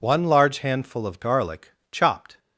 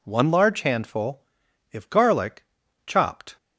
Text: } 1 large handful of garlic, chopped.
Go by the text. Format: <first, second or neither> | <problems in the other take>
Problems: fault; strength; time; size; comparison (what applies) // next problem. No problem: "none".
first | says "if" for "of"; at 1.7 s